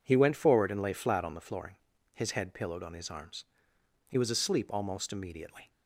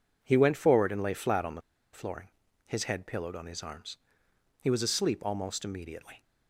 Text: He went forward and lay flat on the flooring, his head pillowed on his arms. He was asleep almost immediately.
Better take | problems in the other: first | pauses between "the" and "flooring"; slight; at 1.6 s; 0.32 s long

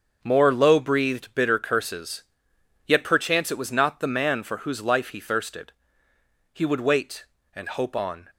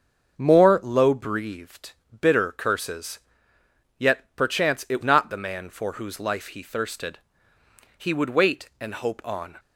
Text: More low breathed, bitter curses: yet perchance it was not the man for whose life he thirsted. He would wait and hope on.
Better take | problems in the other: first | starts louder than the rest; until 1.4 s; 6.5 dB; also in the first // skips "was"; at 5.0 s

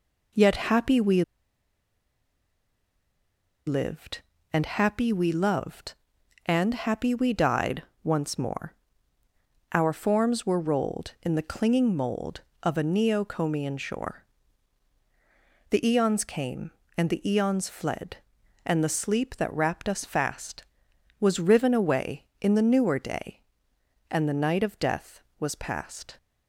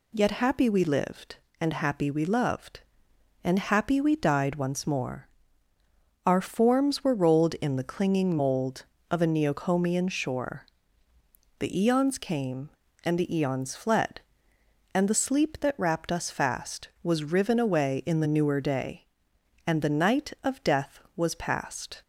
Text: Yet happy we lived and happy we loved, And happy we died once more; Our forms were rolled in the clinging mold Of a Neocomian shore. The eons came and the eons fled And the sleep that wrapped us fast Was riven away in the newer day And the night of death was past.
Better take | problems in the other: second | pauses between "we" and "lived"; strong; at 1.2 s; 2.4 s long // pauses between "died" and "once"; slight; at 7.8 s; 0.20 s long

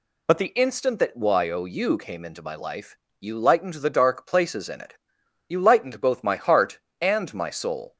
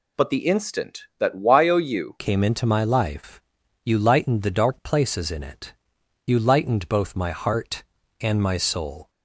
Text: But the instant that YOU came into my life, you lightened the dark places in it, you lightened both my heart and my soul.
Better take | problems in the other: first | changes voice at "came"; from 2.1 s on; 6.9 s long

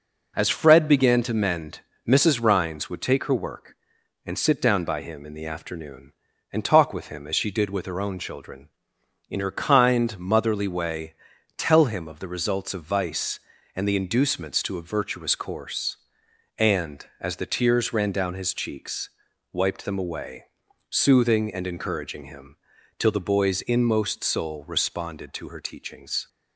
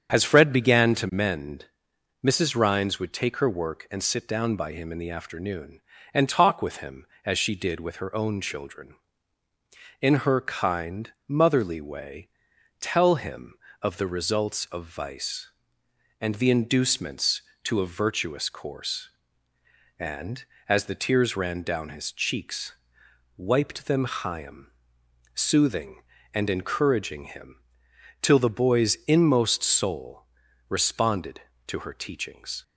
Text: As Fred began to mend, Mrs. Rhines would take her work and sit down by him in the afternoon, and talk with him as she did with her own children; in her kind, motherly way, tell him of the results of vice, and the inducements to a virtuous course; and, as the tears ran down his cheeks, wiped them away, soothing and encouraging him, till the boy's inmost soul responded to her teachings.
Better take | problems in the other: first | starts louder than the rest; strong; until 1.1 s; 7.5 dB // says "chaim" for "away"; at 24.0 s // pauses between "soul" and "responded"; at 30.2 s; 0.42 s long

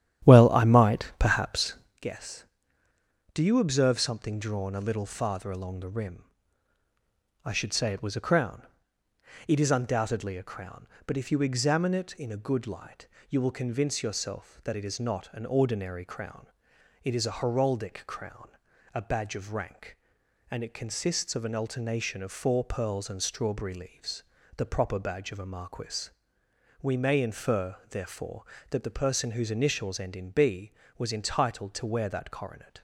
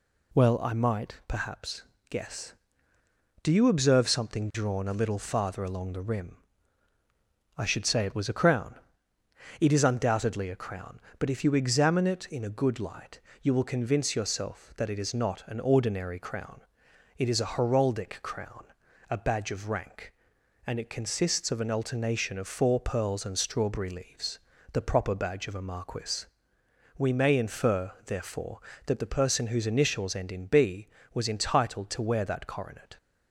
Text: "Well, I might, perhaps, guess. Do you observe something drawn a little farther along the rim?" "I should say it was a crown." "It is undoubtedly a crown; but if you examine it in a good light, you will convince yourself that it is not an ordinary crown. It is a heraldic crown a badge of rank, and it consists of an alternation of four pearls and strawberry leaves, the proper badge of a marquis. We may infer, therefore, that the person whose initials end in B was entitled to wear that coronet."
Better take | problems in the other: second | starts louder than the rest; strong; until 2.1 s; 11 dB // pauses between "crown" and "a"; at 18.4 s; 0.44 s long; also in the second

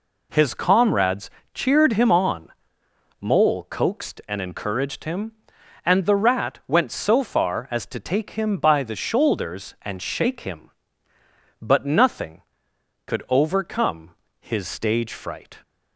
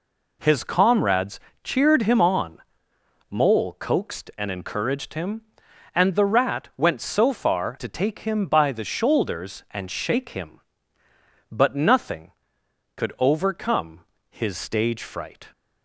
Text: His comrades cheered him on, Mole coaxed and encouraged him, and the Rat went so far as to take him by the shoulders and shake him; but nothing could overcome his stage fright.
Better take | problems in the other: first | pauses between "comrades" and "cheered"; slight; at 1.3 s; 0.24 s long; slight in the first // skips "as"; at 7.7 s // pauses between "overcome" and "his"; slight; at 14.0 s; 0.26 s long; slight in the first

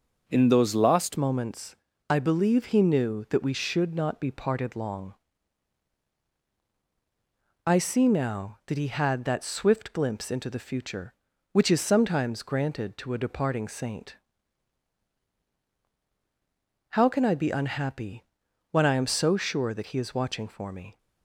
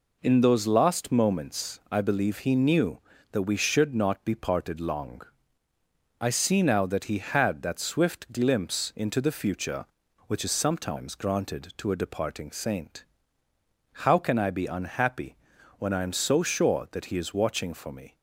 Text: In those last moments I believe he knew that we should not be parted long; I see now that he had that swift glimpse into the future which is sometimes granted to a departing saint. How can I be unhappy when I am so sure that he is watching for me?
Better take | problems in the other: second | changes voice at "moments"; from 1.1 s on; 19.8 s long // pauses between "moments" and "I"; slight; at 1.7 s; 0.34 s long // pauses between "unhappy" and "when"; noticeable; at 18.2 s; 0.46 s long; also in the second

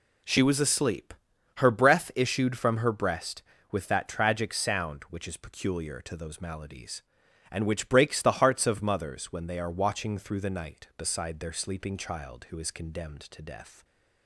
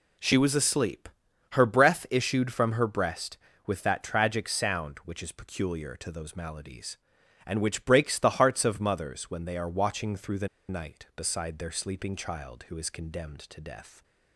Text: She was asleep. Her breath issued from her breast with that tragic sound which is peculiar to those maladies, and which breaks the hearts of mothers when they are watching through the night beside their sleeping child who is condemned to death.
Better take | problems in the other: first | pauses between "the" and "night"; slight; at 10.4 s; 0.20 s long

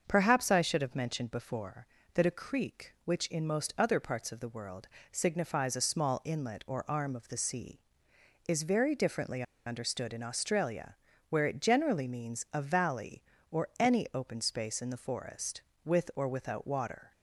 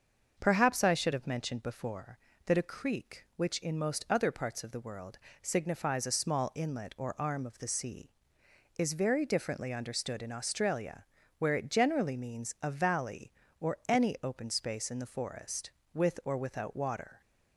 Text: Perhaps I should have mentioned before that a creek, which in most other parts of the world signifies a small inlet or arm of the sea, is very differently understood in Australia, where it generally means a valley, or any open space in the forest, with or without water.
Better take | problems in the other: second | starts louder than the rest; until 1.0 s; 6.5 dB; also in the second // pauses between "world" and "signifies"; slight; at 4.8 s; 0.24 s long; slight in the second // pauses between "differently" and "understood"; slight; at 9.4 s; 0.24 s long

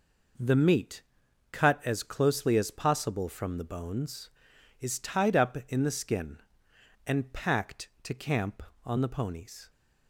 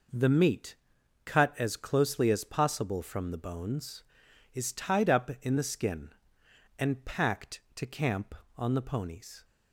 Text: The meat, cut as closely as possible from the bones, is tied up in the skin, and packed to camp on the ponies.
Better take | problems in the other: neither | none

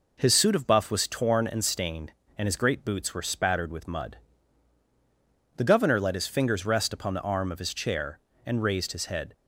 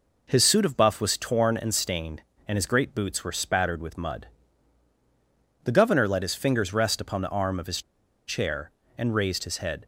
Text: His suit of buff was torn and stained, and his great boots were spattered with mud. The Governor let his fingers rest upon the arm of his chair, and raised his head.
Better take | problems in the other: first | pauses between "his" and "chair"; noticeable; at 7.8 s; 0.46 s long

